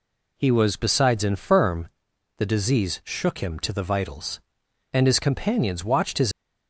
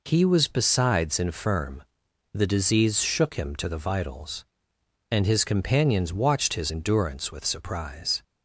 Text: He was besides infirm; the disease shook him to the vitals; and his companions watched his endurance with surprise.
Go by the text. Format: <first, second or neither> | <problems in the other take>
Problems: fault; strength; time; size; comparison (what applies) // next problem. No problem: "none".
second | stops before "endurance with surprise"; at 6.3 s